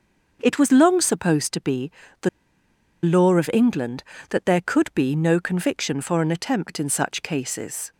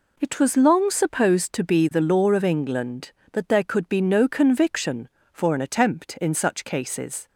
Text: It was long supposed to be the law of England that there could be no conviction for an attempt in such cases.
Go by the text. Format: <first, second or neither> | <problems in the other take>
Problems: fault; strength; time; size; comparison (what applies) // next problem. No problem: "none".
second | starts louder than the rest; until 1.4 s; 6.5 dB // pauses between "be" and "the"; slight; at 1.9 s; 0.32 s long // pauses between "the" and "law"; noticeable; at 2.2 s; 0.75 s long